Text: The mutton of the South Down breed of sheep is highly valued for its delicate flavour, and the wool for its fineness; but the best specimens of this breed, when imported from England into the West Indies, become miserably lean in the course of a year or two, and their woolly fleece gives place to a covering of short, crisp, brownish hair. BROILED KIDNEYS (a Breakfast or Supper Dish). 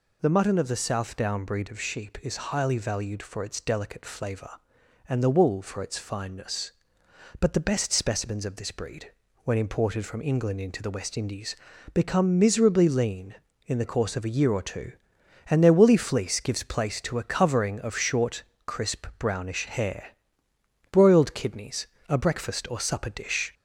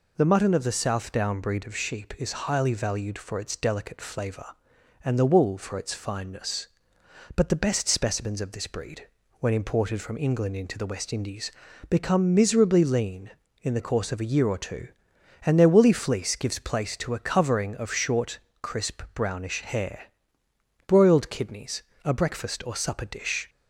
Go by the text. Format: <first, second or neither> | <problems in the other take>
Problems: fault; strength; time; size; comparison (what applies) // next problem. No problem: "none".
second | gets louder; slight; throughout; 3 dB